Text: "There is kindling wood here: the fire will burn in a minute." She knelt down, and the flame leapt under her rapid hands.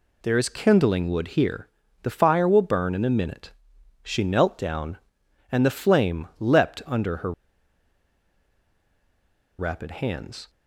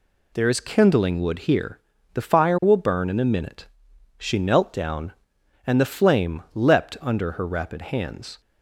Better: second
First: pauses between "her" and "rapid"; strong; at 7.3 s; 2.2 s long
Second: none

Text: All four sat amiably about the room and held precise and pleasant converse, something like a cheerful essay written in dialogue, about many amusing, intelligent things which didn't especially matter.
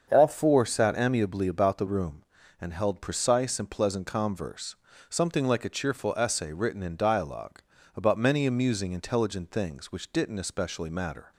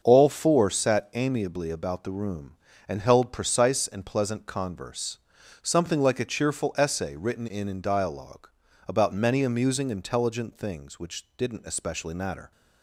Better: first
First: starts louder than the rest; until 1.1 s; 6.5 dB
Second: starts louder than the rest; until 1.0 s; 6.5 dB // says "in" twice; at 7.6 s

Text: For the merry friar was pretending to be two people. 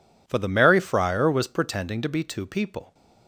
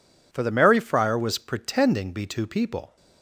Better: first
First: none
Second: skips "to"; at 2.1 s

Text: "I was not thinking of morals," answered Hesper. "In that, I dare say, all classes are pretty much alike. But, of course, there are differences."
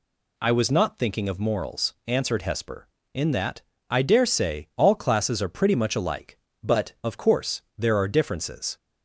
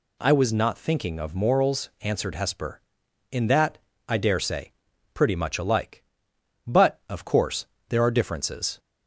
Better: first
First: none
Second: skips "all classes are"; at 4.9 s

